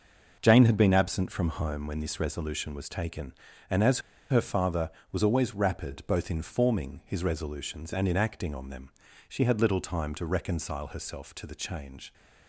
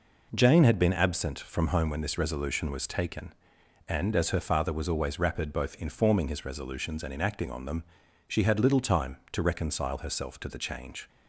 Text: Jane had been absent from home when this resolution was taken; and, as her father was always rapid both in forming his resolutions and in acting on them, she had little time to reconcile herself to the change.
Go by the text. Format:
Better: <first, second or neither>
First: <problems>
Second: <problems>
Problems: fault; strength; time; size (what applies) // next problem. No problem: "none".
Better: second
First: pauses between "as" and "her"; slight; at 3.9 s; 0.31 s long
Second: none